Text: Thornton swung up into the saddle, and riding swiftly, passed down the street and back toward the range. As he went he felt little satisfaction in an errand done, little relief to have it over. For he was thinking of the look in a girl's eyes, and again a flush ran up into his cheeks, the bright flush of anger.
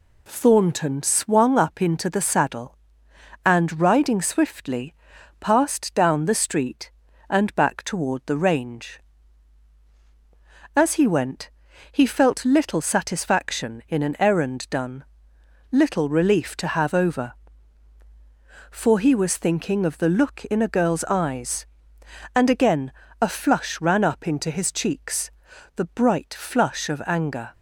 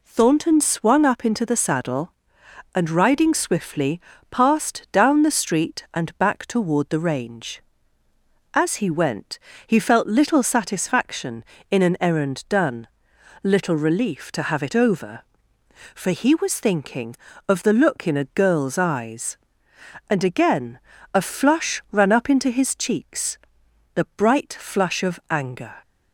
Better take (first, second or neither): second